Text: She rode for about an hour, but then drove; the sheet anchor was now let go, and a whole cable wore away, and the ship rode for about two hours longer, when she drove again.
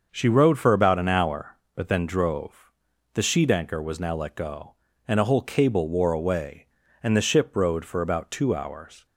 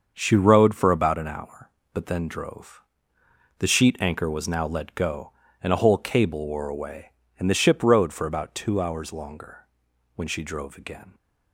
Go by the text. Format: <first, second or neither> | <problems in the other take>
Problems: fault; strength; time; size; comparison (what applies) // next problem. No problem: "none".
second | starts louder than the rest; until 1.1 s; 6.5 dB; also in the second // stops before "longer when she drove again"; at 9.0 s